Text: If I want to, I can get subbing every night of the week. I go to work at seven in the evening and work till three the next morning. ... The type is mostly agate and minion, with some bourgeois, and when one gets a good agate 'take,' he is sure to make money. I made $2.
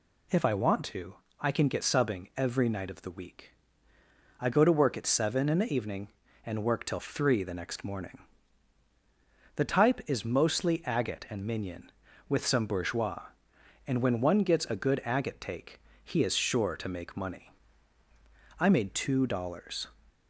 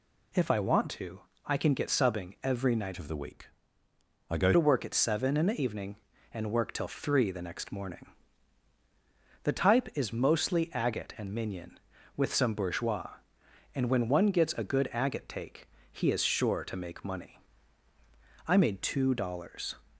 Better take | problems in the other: first | changes voice from "of" to "go"; from 2.9 to 4.5 s; 1.6 s long

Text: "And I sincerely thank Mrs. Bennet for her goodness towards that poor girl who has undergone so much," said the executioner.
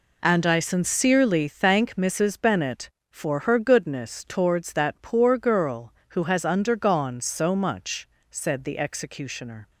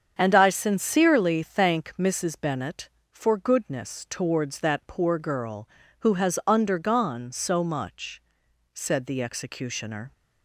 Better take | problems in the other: first | starts louder than the rest; strong; until 1.1 s; 7.5 dB // skips "her"; at 3.3 s

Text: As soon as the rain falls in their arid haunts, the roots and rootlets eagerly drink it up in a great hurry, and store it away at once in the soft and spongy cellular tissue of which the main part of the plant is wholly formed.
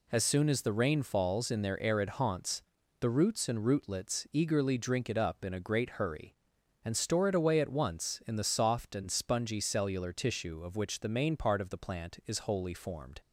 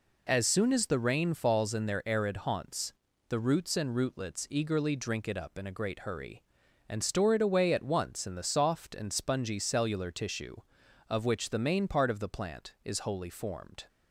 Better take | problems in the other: neither | none

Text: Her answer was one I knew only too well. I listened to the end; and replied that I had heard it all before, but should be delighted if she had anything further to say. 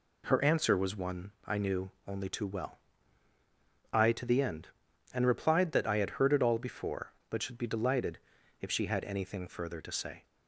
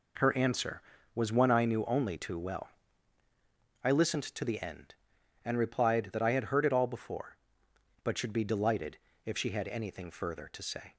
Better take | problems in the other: second | pauses between "knew" and "only"; slight; at 1.9 s; 0.16 s long // skips "listened"; at 4.1 s // pauses between "delighted" and "if"; at 8.1 s; 0.42 s long; slight in the second

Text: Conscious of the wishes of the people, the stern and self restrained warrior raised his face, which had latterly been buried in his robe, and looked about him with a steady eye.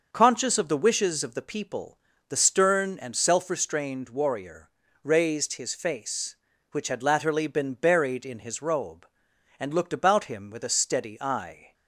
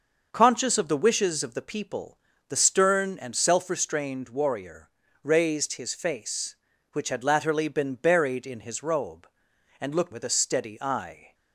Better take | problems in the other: first | starts louder than the rest; noticeable; until 1.3 s; 6 dB // pauses between "warrior" and "raised"; slight; at 4.8 s; 0.36 s long; slight in the first // skips "about him"; at 10.1 s

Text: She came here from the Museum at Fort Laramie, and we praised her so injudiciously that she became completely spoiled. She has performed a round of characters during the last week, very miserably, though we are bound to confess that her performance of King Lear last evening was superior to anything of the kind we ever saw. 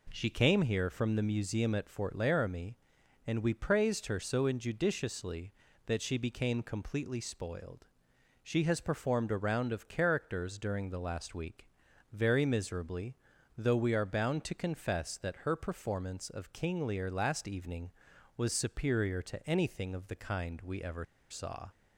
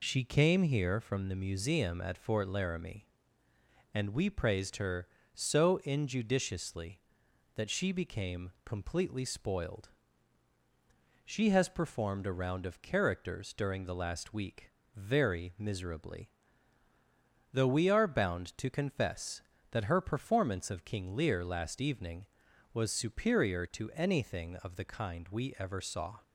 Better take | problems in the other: second | pauses between "ever" and "saw"; slight; at 21.0 s; 0.26 s long

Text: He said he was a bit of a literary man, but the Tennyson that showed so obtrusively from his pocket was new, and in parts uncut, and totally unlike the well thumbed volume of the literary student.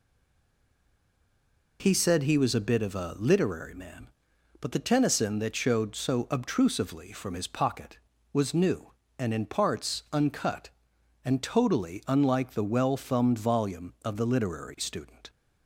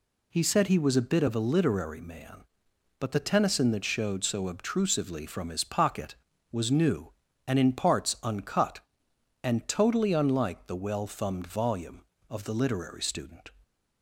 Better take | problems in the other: second | stays silent before the first word; noticeable; until 1.7 s; 1.7 s long

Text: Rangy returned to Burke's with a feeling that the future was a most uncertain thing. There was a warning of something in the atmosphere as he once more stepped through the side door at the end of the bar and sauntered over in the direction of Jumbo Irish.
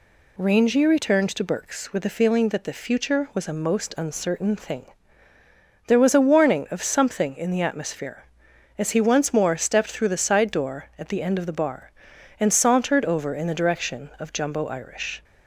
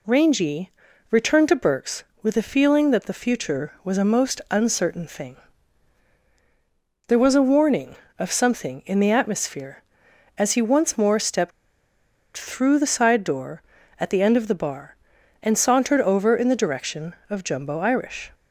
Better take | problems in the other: first | pauses between "Rangy" and "returned"; at 0.7 s; 0.40 s long // pauses between "stepped" and "through"; noticeable; at 11.5 s; 0.85 s long

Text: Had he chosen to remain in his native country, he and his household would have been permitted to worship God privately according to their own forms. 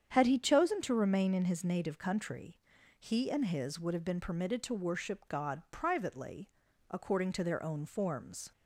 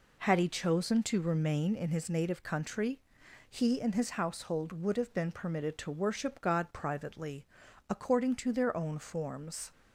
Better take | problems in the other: second | starts louder than the rest; strong; until 1.1 s; 8.5 dB // skips "household"; at 3.7 s // pauses between "privately" and "according"; at 6.4 s; 0.40 s long; also in the second

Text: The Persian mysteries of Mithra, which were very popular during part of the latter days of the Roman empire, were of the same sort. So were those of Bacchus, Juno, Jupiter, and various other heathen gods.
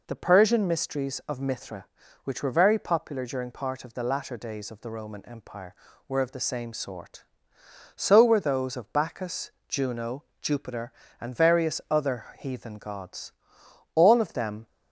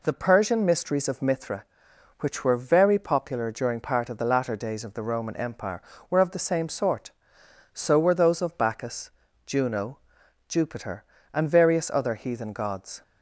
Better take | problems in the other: second | goes on to say "All of them"; noticeable; from 13.9 s on; 0.72 s long

